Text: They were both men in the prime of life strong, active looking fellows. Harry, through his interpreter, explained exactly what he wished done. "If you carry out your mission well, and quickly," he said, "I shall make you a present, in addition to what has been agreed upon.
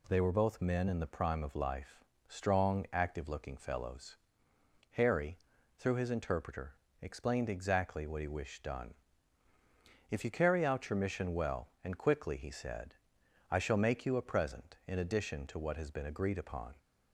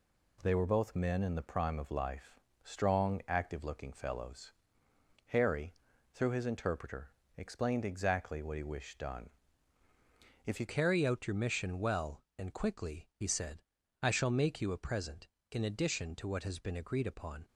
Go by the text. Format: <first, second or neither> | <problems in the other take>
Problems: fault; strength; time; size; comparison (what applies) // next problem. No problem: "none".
first | pauses between "life" and "strong"; slight; at 2.3 s; 0.24 s long; slight in the first // changes voice at "carry"; from 10.6 s on; 6.8 s long